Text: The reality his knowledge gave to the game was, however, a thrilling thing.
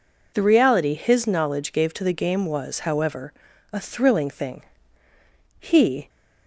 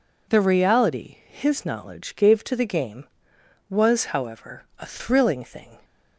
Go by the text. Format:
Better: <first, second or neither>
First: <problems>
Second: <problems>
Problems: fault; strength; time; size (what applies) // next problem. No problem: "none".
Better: second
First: goes on to say "He"; from 5.5 s on; 0.50 s long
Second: none